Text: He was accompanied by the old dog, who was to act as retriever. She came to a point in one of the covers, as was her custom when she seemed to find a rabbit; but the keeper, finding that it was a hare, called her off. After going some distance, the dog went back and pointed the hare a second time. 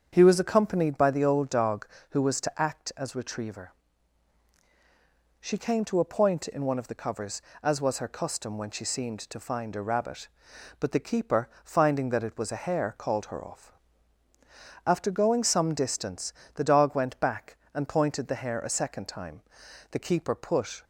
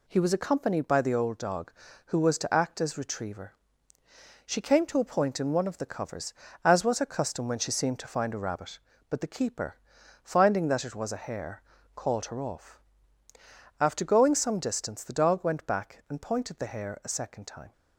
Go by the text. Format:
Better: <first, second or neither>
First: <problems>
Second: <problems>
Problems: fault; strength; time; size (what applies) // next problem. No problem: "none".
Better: second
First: starts louder than the rest; strong; until 1.1 s; 7.5 dB // goes on to say "The keeper put"; noticeable; from 19.8 s on; 0.94 s long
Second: none